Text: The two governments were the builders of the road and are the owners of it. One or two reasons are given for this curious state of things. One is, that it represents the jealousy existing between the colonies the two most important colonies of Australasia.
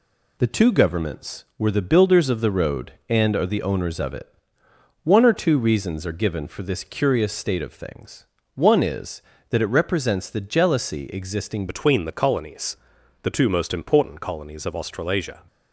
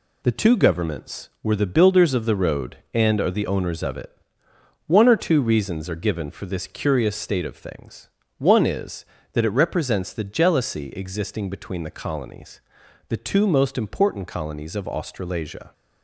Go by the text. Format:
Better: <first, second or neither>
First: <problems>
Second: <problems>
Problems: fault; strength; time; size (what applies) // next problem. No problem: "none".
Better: second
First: changes voice at "between"; from 11.6 s on; 3.8 s long // pauses between "colonies" and "the"; noticeable; at 12.7 s; 0.46 s long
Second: pauses between "colonies" and "the"; noticeable; at 12.5 s; 0.50 s long